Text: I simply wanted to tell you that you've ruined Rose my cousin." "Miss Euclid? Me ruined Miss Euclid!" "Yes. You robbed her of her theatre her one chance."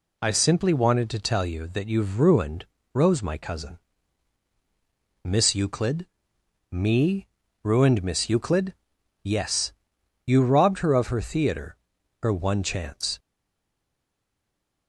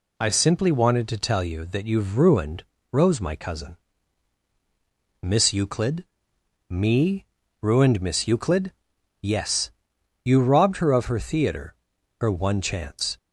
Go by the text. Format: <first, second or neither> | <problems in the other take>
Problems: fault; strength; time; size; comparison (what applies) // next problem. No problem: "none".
second | pauses between "ruined" and "Rose"; slight; at 2.6 s; 0.26 s long; slight in the second // pauses between "Me" and "ruined"; at 7.2 s; 0.38 s long; also in the second // pauses between "theatre" and "her"; noticeable; at 11.7 s; 0.46 s long; noticeable in the second // stays silent after the last word; noticeable; from 13.1 s on; 1.7 s long